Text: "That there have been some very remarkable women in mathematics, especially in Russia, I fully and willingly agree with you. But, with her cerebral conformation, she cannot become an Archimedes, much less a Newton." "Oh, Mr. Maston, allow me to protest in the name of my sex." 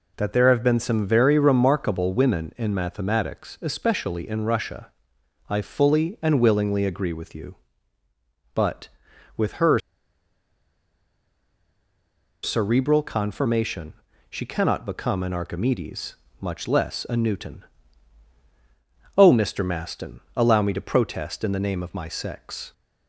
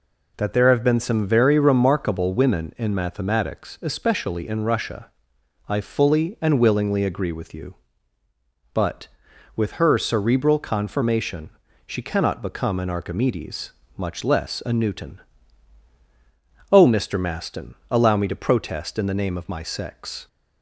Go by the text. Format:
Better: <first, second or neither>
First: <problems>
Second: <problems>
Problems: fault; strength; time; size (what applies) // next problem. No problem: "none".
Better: second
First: pauses between "her" and "cerebral"; strong; at 9.7 s; 2.6 s long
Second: none